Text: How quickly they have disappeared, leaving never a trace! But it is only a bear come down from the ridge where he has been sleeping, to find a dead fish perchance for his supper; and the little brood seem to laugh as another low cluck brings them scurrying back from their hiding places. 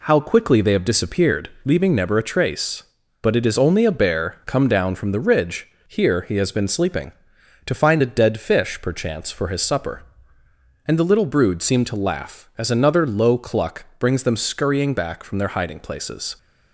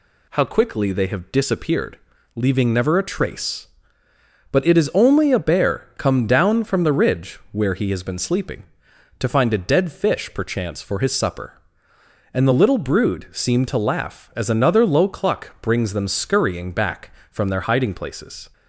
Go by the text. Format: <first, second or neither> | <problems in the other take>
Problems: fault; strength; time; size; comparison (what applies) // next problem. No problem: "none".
second | says "here" for "where"; at 5.8 s // pauses between "cluck" and "brings"; slight; at 13.8 s; 0.16 s long